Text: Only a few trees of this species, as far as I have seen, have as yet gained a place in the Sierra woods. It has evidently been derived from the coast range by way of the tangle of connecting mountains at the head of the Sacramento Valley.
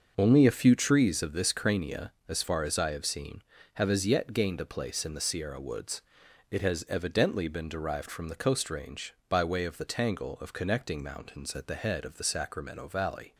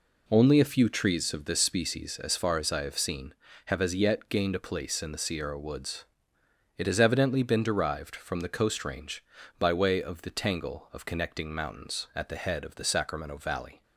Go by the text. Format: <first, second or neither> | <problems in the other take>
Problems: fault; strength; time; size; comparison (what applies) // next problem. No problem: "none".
second | starts louder than the rest; until 1.1 s; 6.5 dB // says "crania" for "species"; at 1.5 s